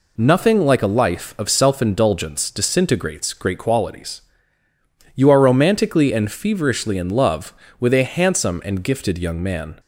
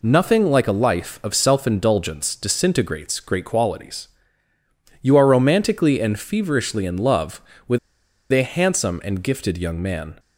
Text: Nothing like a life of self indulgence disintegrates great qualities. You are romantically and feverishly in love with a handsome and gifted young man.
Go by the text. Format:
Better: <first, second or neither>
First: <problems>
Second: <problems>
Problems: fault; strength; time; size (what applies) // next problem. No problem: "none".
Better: first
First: none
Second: pauses between "with" and "a"; noticeable; at 7.7 s; 0.54 s long